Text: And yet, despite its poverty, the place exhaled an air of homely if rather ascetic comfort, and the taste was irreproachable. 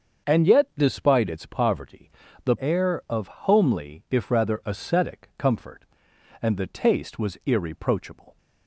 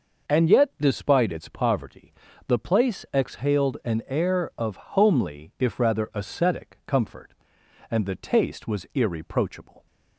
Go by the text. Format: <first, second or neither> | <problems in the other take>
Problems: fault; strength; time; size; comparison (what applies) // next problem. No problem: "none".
second | starts louder than the rest; until 1.3 s; 6.5 dB // skips "place exhaled an"; at 2.5 s